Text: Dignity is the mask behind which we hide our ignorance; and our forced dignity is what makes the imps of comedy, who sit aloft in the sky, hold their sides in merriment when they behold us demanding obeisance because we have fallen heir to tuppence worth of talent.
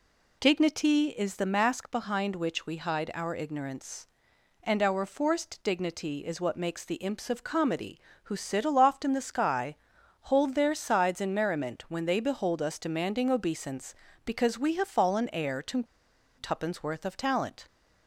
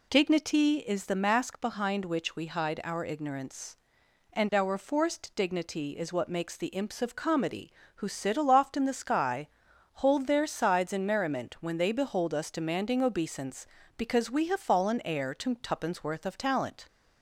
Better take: second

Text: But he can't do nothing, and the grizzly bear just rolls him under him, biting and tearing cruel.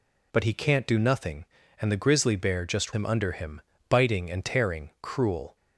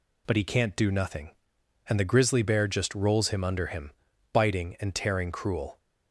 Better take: second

